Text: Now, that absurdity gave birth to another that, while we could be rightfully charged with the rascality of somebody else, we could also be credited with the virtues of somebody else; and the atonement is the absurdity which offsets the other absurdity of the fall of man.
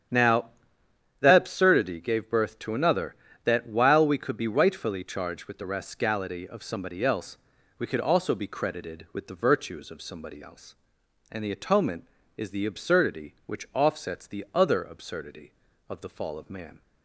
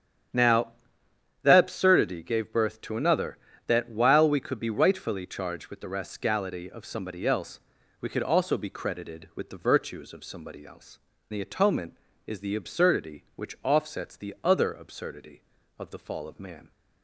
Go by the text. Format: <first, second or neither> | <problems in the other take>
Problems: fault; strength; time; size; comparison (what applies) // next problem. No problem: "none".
first | starts louder than the rest; strong; until 2.0 s; 9 dB; strong in the first // skips "and"; at 11.1 s